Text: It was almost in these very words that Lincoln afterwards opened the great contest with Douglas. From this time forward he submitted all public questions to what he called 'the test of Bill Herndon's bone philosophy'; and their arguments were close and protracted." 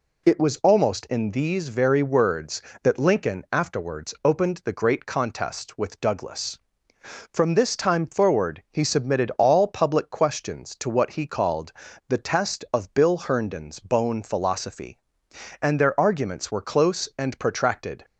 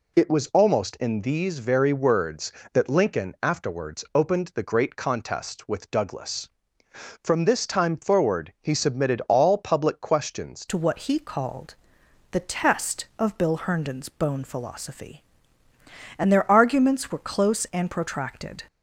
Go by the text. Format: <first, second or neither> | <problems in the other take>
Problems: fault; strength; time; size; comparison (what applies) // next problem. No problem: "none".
first | changes voice at "to"; from 10.6 s on; 8.0 s long // pauses between "called" and "the"; noticeable; at 11.7 s; 0.60 s long; slight in the first